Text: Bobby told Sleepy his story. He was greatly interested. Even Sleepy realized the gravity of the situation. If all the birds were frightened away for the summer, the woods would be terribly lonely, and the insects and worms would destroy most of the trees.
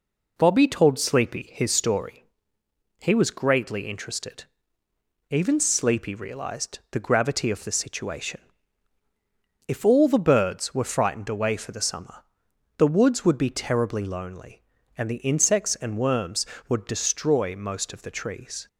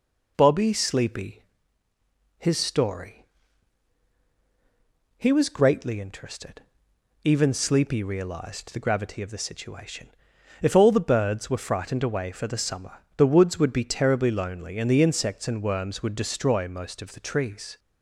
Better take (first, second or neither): first